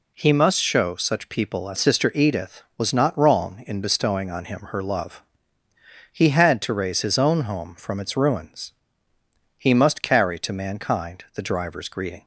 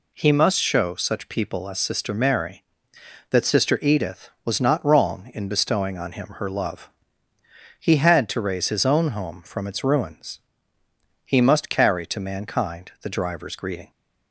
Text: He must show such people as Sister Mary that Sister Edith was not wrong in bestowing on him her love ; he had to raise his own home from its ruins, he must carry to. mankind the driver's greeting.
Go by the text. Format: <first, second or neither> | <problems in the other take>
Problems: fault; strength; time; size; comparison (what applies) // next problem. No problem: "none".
second | skips "Sister Mary that"; at 1.7 s